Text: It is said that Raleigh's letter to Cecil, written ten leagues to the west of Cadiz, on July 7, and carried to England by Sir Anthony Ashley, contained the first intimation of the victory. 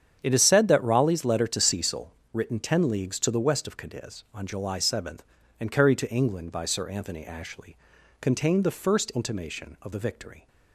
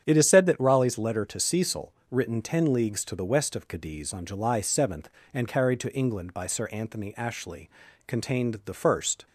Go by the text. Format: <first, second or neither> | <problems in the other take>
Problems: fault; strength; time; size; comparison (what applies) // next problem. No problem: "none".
first | starts louder than the rest; strong; until 1.0 s; 8.5 dB; strong in the first // stops before "intimation of the victory"; at 9.2 s